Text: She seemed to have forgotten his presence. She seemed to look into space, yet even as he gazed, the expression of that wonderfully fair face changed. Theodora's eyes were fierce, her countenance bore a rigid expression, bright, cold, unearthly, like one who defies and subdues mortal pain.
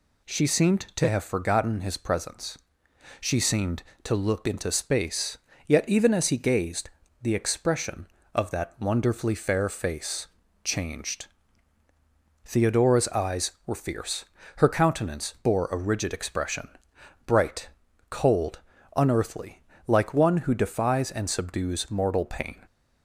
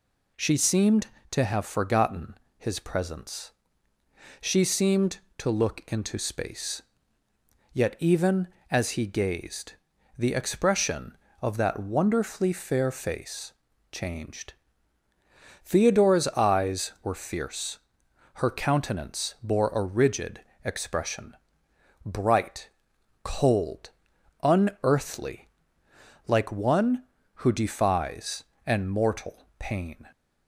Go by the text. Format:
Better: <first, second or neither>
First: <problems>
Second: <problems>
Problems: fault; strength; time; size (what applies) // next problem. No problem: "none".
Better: first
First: pauses between "face" and "changed"; slight; at 10.2 s; 0.36 s long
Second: pauses between "forgotten" and "his"; slight; at 2.3 s; 0.22 s long // pauses between "face" and "changed"; at 13.5 s; 0.40 s long // pauses between "rigid" and "expression"; slight; at 20.3 s; 0.24 s long // skips "subdues"; at 28.8 s